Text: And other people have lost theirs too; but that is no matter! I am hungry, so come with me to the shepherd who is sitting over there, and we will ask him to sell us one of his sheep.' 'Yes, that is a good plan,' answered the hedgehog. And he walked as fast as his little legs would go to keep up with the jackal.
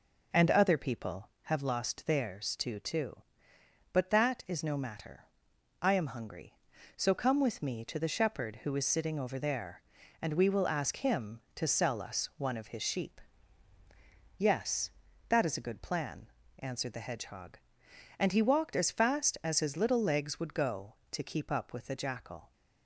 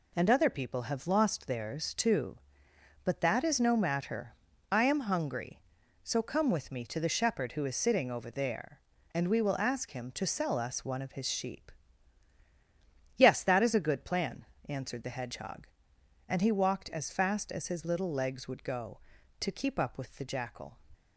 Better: second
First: says "too" twice; at 2.7 s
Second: none

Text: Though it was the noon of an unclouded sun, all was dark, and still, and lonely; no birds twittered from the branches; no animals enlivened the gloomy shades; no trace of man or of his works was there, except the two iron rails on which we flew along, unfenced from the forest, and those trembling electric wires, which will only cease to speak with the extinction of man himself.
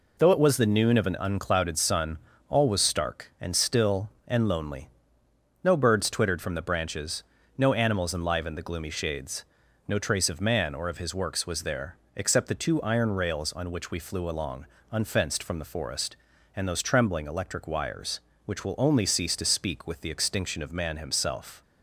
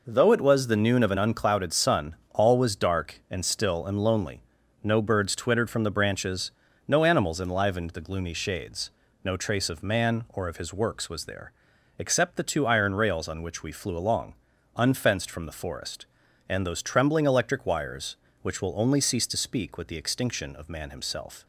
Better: second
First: says "stark" for "dark"; at 2.7 s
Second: none

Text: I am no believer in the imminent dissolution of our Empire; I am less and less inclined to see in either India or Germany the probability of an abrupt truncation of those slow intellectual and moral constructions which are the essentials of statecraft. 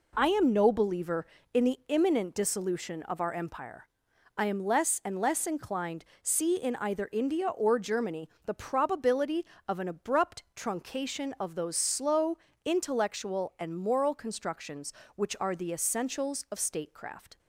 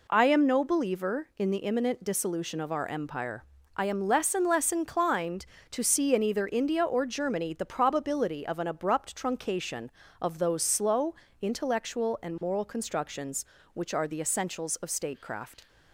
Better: second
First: skips "to"; at 6.1 s // pauses between "Germany" and "the"; slight; at 8.2 s; 0.16 s long // pauses between "slow" and "intellectual"; slight; at 12.3 s; 0.26 s long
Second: pauses between "slow" and "intellectual"; slight; at 11.1 s; 0.26 s long

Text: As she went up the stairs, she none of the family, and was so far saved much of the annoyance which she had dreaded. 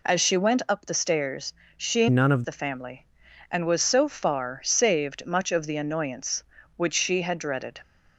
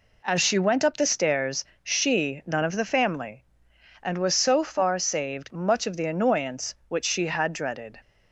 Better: second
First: changes voice from "none" to "of"; from 2.0 to 2.4 s; 0.4 s long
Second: none

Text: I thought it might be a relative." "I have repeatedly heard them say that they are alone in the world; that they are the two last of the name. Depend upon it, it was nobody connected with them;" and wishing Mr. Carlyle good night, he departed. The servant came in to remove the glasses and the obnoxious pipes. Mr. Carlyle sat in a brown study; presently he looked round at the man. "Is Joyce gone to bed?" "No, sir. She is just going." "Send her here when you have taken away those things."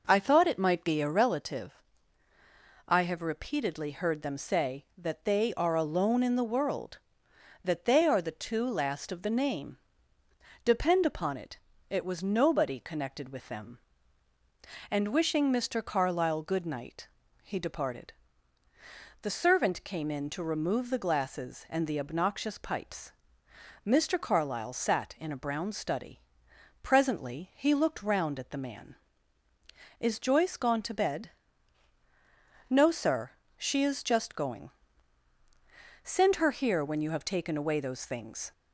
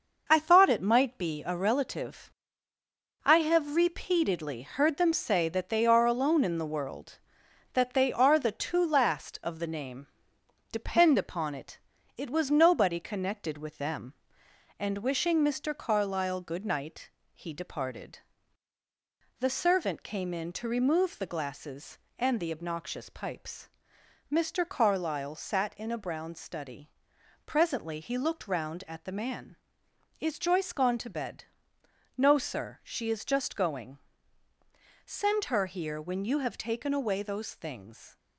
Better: first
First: none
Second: gets quieter; noticeable; throughout; 6 dB

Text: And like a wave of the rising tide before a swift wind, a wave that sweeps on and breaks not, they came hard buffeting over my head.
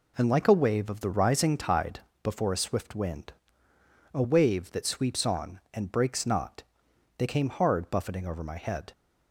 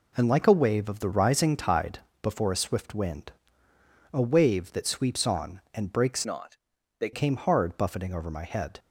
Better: first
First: pauses between "tide" and "before"; slight; at 2.0 s; 0.22 s long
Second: pauses between "tide" and "before"; slight; at 1.9 s; 0.22 s long // changes voice from "not" to "they"; from 6.2 to 7.1 s; 0.9 s long

